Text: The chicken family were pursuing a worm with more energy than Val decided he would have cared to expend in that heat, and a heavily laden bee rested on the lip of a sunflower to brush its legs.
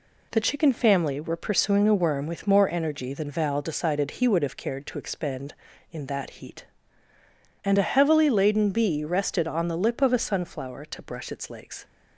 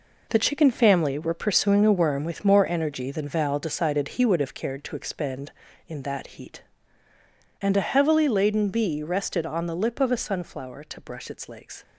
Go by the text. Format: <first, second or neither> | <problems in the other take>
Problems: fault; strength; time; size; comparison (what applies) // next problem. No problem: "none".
first | gets quieter; strong; throughout; 9 dB